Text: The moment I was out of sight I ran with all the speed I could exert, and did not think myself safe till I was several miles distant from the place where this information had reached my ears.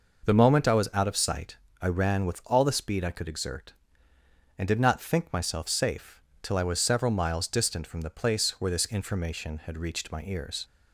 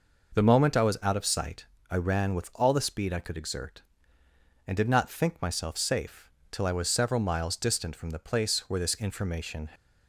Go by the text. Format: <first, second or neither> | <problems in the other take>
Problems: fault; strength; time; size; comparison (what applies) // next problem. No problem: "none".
first | pauses between "sight" and "I"; slight; at 1.6 s; 0.26 s long; slight in the first // pauses between "safe" and "till"; slight; at 6.2 s; 0.22 s long; slight in the first // stops before "had reached my ears"; at 9.7 s